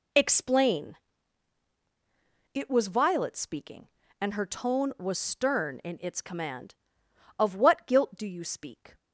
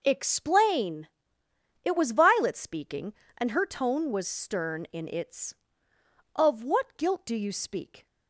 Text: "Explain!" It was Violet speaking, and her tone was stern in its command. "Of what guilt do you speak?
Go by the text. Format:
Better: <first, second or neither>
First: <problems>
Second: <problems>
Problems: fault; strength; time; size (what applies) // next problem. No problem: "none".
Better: first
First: none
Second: skips "command"; at 5.9 s